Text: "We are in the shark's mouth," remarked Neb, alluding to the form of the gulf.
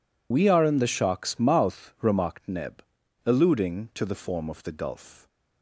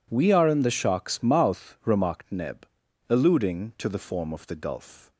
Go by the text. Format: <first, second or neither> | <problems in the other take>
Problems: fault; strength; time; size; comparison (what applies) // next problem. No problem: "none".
second | loses the start of "We"; at 0.3 s; 50 ms